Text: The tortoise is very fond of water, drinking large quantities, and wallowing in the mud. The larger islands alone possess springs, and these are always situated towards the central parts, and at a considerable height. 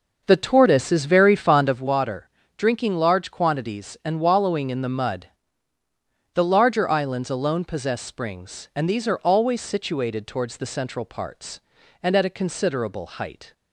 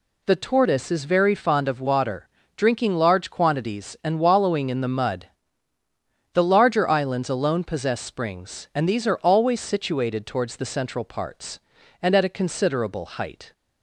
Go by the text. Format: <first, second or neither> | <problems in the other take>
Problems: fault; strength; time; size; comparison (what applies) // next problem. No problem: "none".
second | starts louder than the rest; noticeable; until 1.9 s; 6 dB